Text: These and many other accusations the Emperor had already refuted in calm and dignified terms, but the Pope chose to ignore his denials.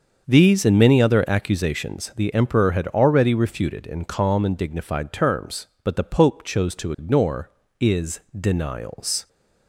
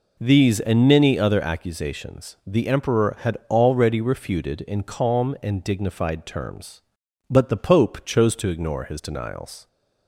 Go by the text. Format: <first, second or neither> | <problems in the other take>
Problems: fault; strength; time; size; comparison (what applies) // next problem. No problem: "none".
second | starts louder than the rest; until 1.3 s; 6.5 dB // says "is" for "his"; at 7.7 s